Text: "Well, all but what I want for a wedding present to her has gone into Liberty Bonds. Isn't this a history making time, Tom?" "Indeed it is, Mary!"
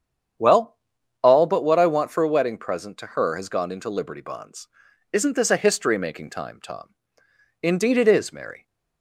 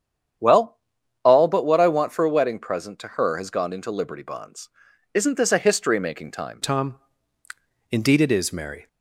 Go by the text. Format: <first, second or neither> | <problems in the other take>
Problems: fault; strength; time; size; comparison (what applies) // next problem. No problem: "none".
first | starts louder than the rest; strong; until 1.8 s; 8.5 dB; strong in the first // changes voice at "Tom"; from 6.6 s on; 2.2 s long